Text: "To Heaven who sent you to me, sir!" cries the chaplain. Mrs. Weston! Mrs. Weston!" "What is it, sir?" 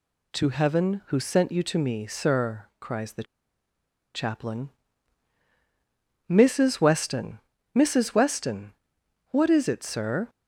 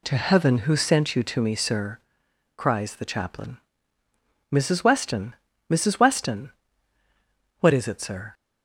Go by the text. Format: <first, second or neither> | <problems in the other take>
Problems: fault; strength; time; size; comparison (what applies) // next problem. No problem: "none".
second | pauses between "the" and "chaplain"; noticeable; at 3.2 s; 0.91 s long